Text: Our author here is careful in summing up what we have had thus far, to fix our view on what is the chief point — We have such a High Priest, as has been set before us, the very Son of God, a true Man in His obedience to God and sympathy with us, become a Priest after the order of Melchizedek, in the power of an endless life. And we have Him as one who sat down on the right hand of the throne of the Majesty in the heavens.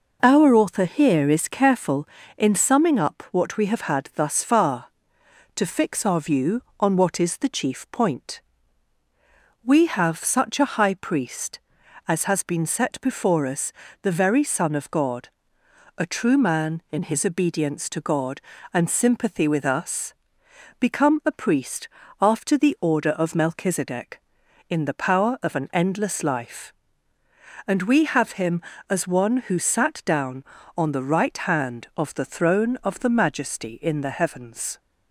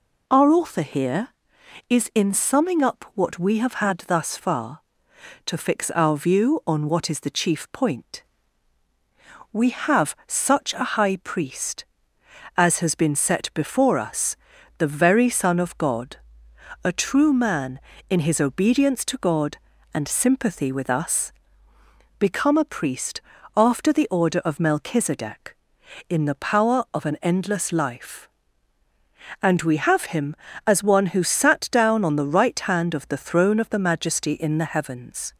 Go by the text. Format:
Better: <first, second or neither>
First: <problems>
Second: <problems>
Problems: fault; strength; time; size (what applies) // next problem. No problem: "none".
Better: first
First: pauses between "Priest" and "after"; slight; at 21.8 s; 0.32 s long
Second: skips "careful"; at 2.1 s // pauses between "Priest" and "after"; slight; at 23.2 s; 0.34 s long